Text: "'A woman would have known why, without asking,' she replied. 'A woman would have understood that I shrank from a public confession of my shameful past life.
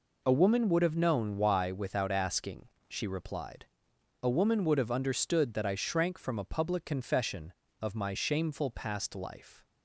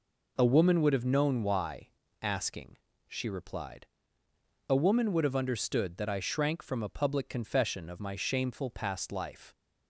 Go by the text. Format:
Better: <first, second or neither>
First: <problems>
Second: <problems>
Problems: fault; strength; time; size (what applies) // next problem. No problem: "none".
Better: first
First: none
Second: skips "without"; at 2.0 s